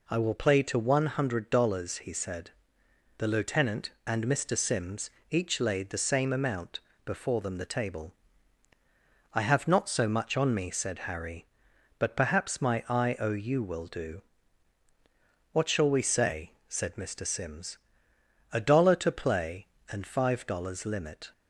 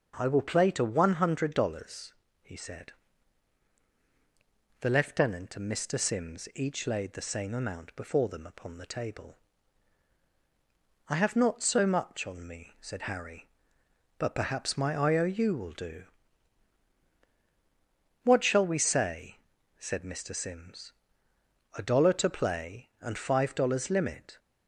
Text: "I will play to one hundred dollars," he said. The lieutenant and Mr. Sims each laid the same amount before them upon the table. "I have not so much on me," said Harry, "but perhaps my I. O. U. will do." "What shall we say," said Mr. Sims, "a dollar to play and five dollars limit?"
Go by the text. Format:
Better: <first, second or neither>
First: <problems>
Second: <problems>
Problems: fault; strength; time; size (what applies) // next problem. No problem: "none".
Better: second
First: pauses between "Sims" and "each"; slight; at 5.0 s; 0.20 s long // pauses between "amount" and "before"; slight; at 6.7 s; 0.26 s long // skips "upon"; at 7.5 s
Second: none